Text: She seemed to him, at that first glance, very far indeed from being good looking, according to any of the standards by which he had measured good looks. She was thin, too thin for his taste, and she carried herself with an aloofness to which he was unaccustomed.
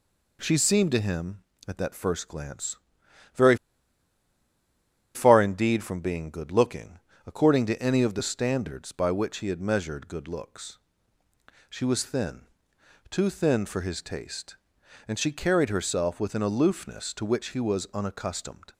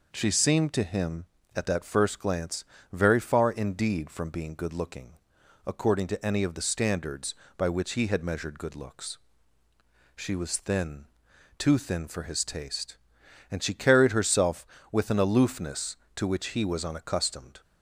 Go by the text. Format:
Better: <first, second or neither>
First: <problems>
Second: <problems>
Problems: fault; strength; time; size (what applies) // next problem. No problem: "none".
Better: second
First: pauses between "very" and "far"; strong; at 3.5 s; 1.5 s long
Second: none